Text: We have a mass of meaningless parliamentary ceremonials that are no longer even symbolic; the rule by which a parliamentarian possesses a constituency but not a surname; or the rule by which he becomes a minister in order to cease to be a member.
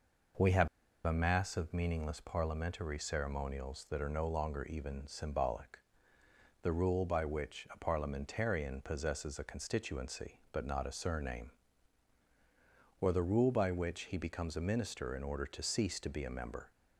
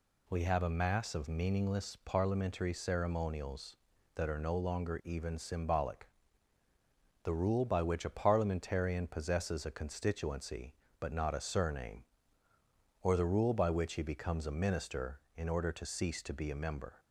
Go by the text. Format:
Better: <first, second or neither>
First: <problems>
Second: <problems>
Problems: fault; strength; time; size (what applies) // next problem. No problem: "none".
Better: second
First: pauses between "have" and "a"; at 0.6 s; 0.36 s long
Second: none